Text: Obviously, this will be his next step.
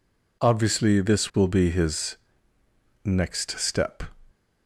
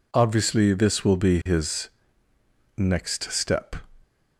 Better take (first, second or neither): neither